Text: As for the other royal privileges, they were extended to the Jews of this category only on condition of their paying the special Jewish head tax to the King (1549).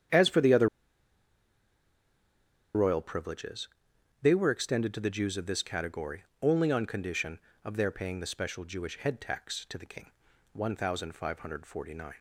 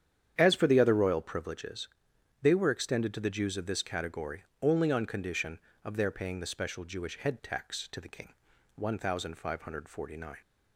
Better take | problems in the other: second | starts louder than the rest; strong; until 3.2 s; 9 dB; strong in the second // pauses between "other" and "royal"; strong; at 0.6 s; 2.0 s long // pauses between "category" and "only"; slight; at 6.2 s; 0.18 s long; slight in the second

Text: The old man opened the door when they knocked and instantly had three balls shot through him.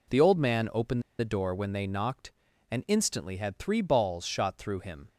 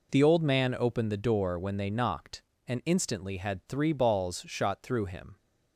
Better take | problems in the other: second | pauses between "opened" and "the"; slight; at 1.0 s; 0.17 s long

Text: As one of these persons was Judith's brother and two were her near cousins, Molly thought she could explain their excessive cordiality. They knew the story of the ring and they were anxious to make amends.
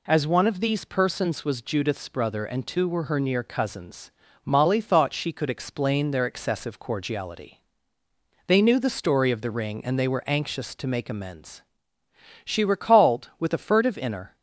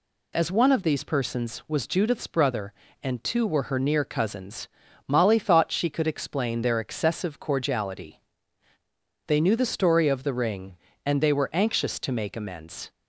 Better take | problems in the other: second | goes on to say "She recalled with a furtive inner"; strong; from 12.4 s on; 1.9 s long

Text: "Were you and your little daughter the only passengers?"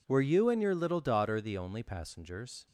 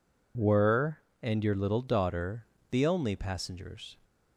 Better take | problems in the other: first | skips "you"; at 1.0 s // pauses between "daughter" and "the"; slight; at 2.4 s; 0.26 s long

